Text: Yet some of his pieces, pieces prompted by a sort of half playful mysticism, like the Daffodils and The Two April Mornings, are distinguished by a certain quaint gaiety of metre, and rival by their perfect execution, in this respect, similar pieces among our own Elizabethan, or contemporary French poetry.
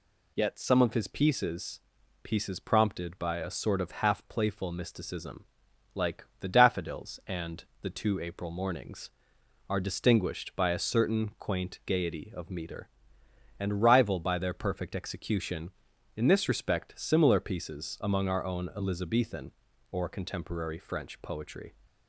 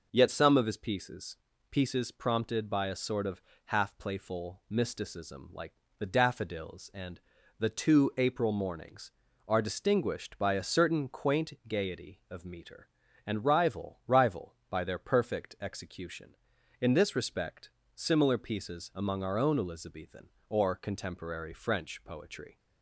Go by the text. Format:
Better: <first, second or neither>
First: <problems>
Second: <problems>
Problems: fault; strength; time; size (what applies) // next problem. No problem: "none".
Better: first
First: pauses between "like" and "the"; slight; at 6.2 s; 0.16 s long // pauses between "and" and "The"; slight; at 7.6 s; 0.18 s long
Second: pauses between "of" and "half"; slight; at 3.4 s; 0.24 s long // pauses between "like" and "the"; slight; at 5.7 s; 0.24 s long // pauses between "and" and "The"; at 7.1 s; 0.38 s long // says "rival" twice; at 14.0 s